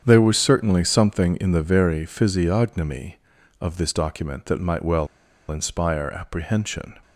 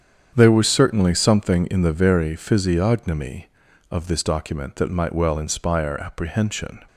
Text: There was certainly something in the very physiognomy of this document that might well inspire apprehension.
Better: second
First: starts louder than the rest; strong; until 1.0 s; 8 dB // pauses between "well" and "inspire"; at 5.0 s; 0.42 s long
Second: starts louder than the rest; strong; until 1.3 s; 8 dB

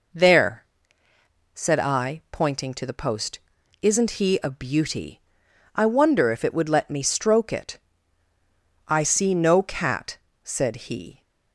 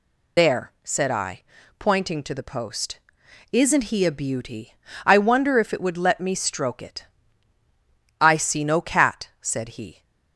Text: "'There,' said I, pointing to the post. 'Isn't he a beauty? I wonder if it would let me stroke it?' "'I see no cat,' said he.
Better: first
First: none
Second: loses the start of "There"; at 0.3 s; 90 ms

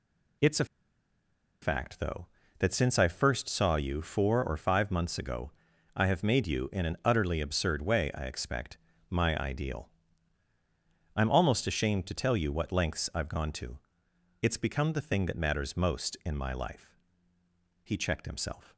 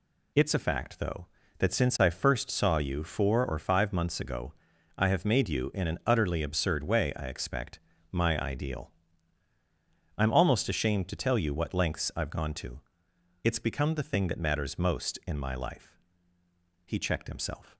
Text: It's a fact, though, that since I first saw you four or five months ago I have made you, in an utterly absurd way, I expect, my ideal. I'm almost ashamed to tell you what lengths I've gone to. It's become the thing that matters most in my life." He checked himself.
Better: second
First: pauses between "a" and "fact"; noticeable; at 0.6 s; 0.97 s long // pauses between "ago" and "I"; at 5.5 s; 0.44 s long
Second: pauses between "ago" and "I"; at 4.5 s; 0.44 s long

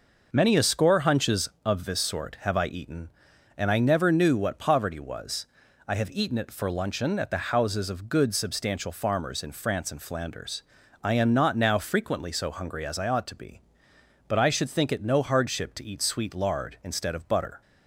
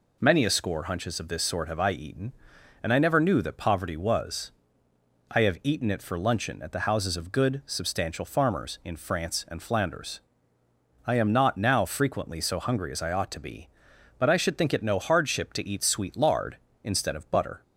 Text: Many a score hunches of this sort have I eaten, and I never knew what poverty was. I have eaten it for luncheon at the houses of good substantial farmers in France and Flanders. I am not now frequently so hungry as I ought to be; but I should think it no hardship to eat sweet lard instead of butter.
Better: first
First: none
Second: says "that" for "what"; at 3.4 s

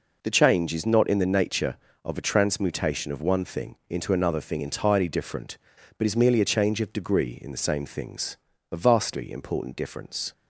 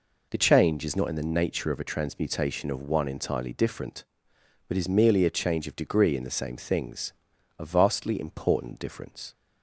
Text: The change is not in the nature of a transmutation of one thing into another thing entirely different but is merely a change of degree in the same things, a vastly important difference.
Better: first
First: none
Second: skips "thing into another thing"; at 3.0 s

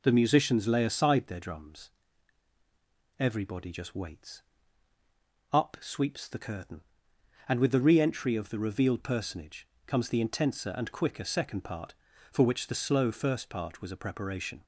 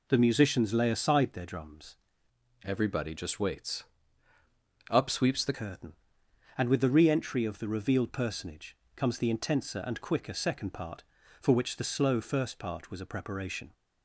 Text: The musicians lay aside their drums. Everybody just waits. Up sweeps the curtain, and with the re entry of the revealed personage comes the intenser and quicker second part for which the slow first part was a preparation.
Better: first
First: pauses between "personage" and "comes"; slight; at 9.6 s; 0.18 s long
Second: changes voice from "Everybody" to "the"; from 2.6 to 5.5 s; 2.9 s long // pauses between "personage" and "comes"; slight; at 8.7 s; 0.18 s long

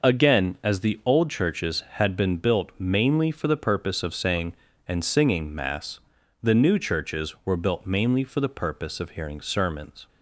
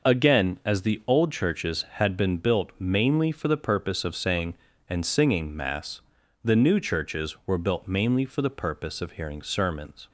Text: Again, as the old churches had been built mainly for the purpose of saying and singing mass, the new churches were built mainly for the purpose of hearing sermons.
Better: neither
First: none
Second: none

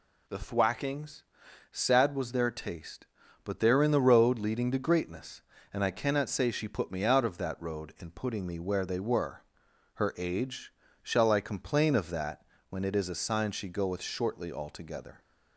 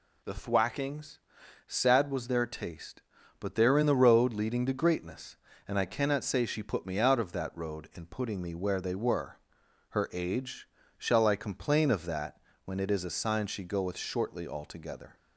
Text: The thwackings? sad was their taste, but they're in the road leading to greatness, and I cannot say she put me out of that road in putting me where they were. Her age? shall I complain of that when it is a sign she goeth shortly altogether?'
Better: neither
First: pauses between "that" and "when"; slight; at 12.4 s; 0.28 s long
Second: pauses between "that" and "when"; slight; at 12.3 s; 0.28 s long

